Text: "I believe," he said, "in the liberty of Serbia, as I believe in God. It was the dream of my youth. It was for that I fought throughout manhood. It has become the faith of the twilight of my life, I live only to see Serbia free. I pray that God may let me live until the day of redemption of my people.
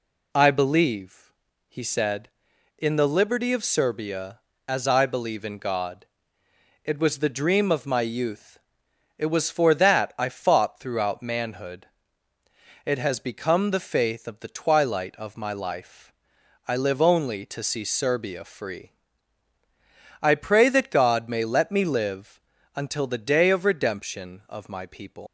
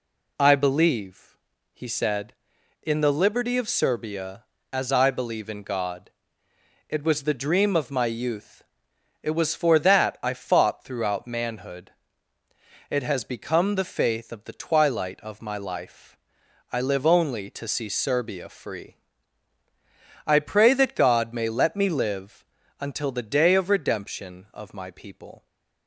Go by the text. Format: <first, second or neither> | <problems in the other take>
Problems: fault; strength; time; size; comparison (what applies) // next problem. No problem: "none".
second | pauses between "live" and "until"; slight; at 22.3 s; 0.34 s long; slight in the second // leaves "people" unfinished; at 25.2 s; 145 ms